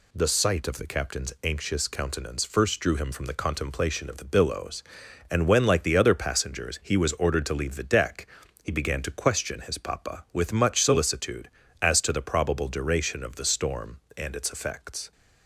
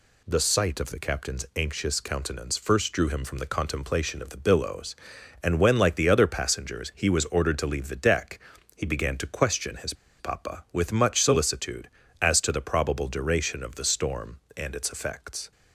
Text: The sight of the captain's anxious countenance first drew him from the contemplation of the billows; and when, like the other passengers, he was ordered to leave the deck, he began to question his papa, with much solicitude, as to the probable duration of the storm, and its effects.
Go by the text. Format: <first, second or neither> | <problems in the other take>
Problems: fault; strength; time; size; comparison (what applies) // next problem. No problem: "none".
first | pauses between "his" and "papa"; slight; at 9.9 s; 0.26 s long